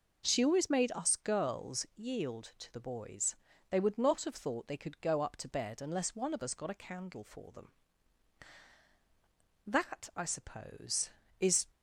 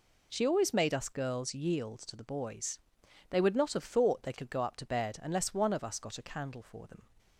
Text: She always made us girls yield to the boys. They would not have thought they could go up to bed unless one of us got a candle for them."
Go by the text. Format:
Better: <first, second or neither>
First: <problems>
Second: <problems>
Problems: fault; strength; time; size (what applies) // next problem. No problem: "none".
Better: second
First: goes on to say "That I suppose is"; strong; from 9.6 s on; 1.9 s long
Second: none